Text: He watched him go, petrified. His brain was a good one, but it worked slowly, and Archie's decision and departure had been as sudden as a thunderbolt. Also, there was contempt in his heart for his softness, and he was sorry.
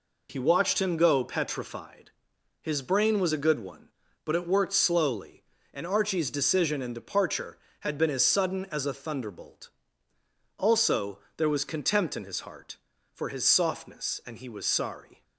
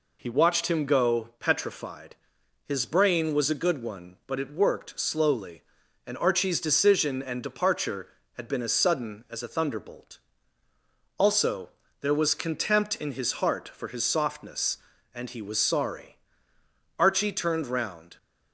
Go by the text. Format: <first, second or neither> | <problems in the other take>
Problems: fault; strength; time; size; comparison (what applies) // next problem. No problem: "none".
first | goes on to say "Archie turned round"; noticeable; from 16.9 s on; 1.1 s long